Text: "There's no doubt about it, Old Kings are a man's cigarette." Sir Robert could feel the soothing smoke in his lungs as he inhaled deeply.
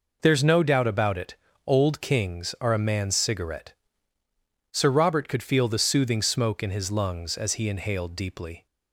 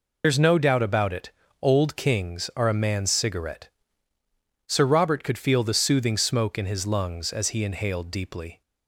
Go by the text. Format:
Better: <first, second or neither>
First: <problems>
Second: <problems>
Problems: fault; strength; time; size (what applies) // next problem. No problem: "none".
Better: first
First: none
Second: loses the start of "There's"; at 0.2 s; 75 ms